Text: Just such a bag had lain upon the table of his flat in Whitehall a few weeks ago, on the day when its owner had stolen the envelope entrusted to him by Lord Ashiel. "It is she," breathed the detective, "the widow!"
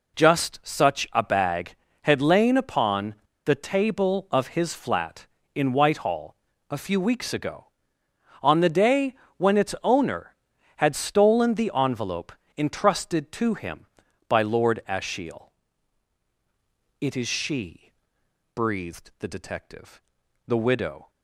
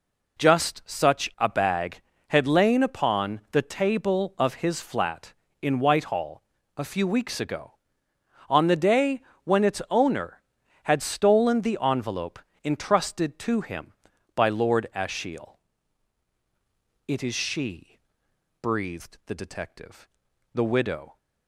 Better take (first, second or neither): second